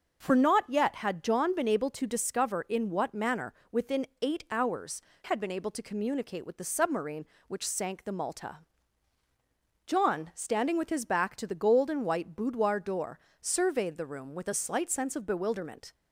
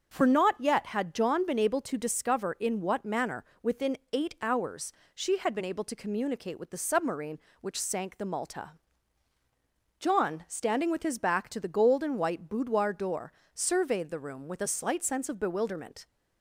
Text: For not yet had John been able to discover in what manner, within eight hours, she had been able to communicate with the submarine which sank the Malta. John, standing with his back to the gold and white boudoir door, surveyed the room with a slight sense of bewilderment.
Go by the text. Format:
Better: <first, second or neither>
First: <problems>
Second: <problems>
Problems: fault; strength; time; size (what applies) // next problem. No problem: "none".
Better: second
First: starts louder than the rest; until 1.2 s; 6.5 dB // pauses between "within" and "eight"; slight; at 4.0 s; 0.16 s long // skips "she"; at 5.1 s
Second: starts louder than the rest; until 1.1 s; 6.5 dB // pauses between "within" and "eight"; slight; at 3.9 s; 0.16 s long